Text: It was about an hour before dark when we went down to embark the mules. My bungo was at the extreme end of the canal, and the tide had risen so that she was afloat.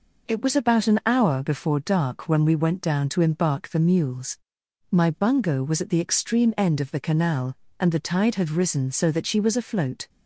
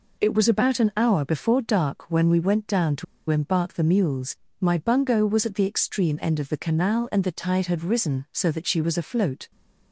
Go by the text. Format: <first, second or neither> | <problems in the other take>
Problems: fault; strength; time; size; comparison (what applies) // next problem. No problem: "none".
first | pauses between "to" and "embark"; slight; at 3.0 s; 0.25 s long